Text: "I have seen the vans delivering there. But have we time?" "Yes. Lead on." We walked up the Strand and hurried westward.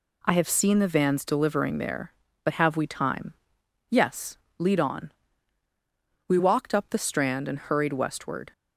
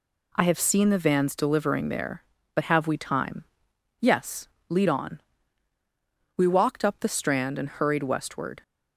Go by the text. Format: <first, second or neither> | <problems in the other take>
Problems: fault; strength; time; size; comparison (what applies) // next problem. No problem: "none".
neither | none